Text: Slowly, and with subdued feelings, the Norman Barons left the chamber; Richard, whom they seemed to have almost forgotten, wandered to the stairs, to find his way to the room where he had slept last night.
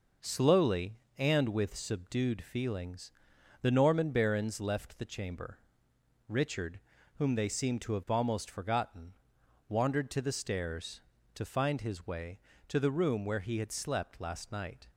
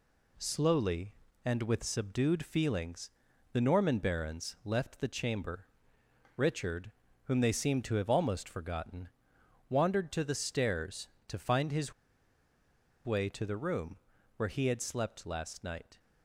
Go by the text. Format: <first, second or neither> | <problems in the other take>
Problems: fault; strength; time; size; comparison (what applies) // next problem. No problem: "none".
first | pauses between "his" and "way"; at 11.9 s; 1.1 s long // pauses between "room" and "where"; at 13.9 s; 0.40 s long